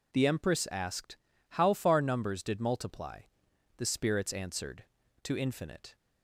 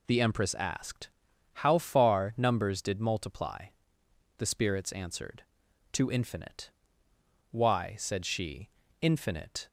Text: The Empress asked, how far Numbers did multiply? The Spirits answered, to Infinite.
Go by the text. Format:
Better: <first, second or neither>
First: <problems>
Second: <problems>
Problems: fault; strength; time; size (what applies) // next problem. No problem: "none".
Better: first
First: none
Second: goes on to say "Why said she Infinite"; strong; from 7.5 s on; 2.1 s long